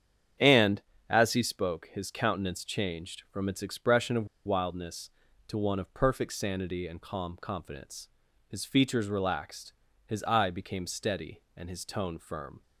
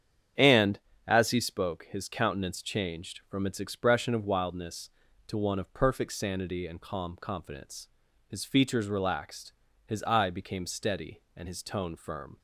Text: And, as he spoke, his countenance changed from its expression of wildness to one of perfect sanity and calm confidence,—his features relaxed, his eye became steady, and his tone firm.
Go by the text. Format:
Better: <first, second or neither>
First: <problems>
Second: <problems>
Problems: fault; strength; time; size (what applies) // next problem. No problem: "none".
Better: second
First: starts louder than the rest; strong; until 1.6 s; 8.5 dB // pauses between "of" and "wildness"; slight; at 4.2 s; 0.18 s long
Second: starts louder than the rest; strong; until 1.6 s; 8.5 dB